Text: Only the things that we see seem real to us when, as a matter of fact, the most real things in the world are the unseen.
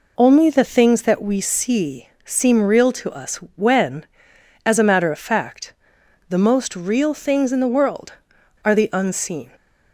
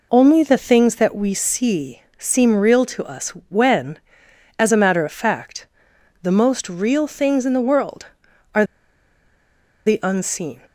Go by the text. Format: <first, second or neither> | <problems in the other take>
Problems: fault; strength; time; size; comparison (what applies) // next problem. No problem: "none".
first | pauses between "see" and "seem"; slight; at 2.0 s; 0.16 s long; slight in the first // pauses between "us" and "when"; slight; at 3.2 s; 0.18 s long; slight in the first // pauses between "are" and "the"; at 8.6 s; 1.2 s long